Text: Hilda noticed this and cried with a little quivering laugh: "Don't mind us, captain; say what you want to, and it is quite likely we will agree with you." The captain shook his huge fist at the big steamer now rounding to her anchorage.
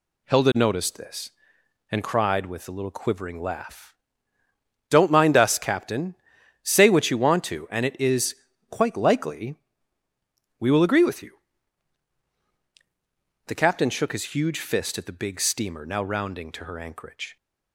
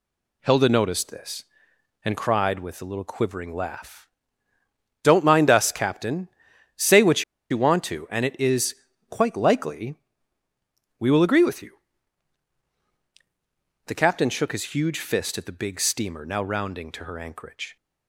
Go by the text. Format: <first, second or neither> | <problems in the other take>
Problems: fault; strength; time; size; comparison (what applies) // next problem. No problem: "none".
first | pauses between "what" and "you"; slight; at 7.2 s; 0.26 s long // pauses between "is" and "quite"; slight; at 8.7 s; 0.36 s long; slight in the first // pauses between "likely" and "we"; at 9.9 s; 1.0 s long; also in the first